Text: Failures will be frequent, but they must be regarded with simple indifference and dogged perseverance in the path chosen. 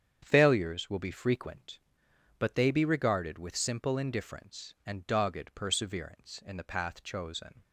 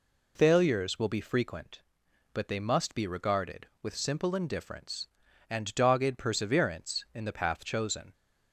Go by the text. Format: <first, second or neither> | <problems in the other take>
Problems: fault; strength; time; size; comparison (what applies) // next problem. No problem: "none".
second | starts louder than the rest; strong; until 1.2 s; 8 dB // skips "must"; at 2.7 s